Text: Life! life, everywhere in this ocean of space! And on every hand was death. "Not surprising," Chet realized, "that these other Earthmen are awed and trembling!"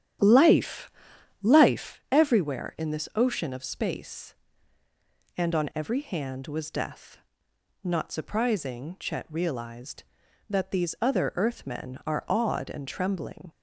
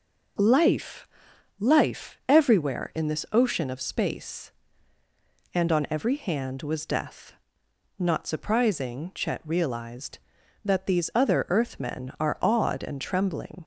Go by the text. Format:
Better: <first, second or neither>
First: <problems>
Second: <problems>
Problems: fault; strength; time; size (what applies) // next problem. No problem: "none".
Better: second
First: starts louder than the rest; strong; until 2.0 s; 10 dB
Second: none